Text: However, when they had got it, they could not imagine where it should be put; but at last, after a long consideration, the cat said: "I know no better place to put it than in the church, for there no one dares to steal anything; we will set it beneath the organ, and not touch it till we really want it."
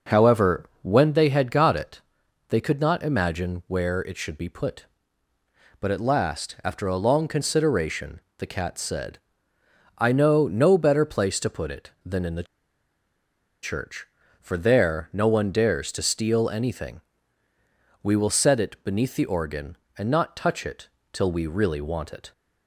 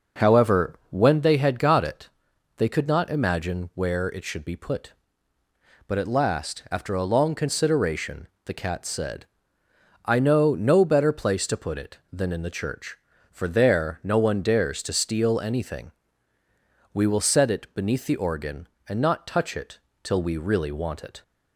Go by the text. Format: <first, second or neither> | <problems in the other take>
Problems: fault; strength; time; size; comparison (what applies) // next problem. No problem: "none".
second | pauses between "the" and "church"; at 12.4 s; 1.1 s long // pauses between "it" and "till"; slight; at 20.8 s; 0.24 s long; slight in the second